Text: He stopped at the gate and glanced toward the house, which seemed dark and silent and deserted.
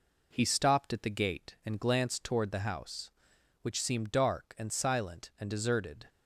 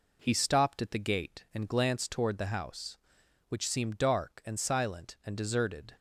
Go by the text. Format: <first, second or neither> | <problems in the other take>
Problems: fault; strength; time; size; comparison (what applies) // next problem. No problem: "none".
neither | none